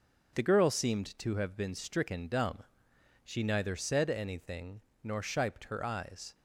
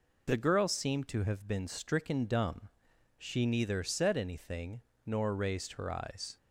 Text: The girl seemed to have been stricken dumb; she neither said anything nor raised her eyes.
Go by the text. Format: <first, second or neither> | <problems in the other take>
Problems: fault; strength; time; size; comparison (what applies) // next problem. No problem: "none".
second | pauses between "anything" and "nor"; slight; at 4.8 s; 0.24 s long; slight in the second // says "shiped" for "raised"; at 5.2 s